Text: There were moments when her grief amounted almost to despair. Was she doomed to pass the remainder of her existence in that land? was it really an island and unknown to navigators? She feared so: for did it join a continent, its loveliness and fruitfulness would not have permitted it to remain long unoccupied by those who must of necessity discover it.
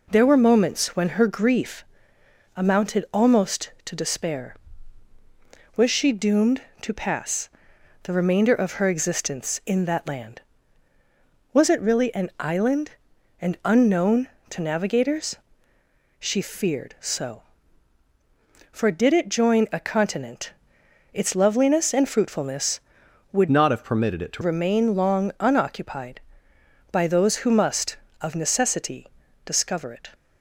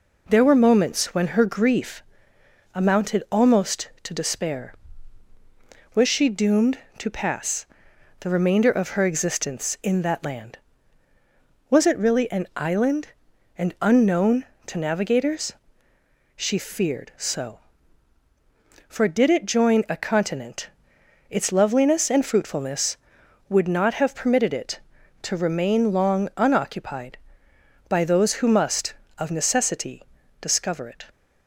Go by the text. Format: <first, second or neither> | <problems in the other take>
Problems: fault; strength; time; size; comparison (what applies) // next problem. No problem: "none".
second | pauses between "grief" and "amounted"; noticeable; at 1.8 s; 0.72 s long; noticeable in the second // pauses between "pass" and "the"; noticeable; at 7.5 s; 0.52 s long; noticeable in the second // changes voice from "not" to "to"; from 23.4 to 24.4 s; 1.0 s long // pauses between "necessity" and "discover"; at 29.0 s; 0.38 s long; also in the second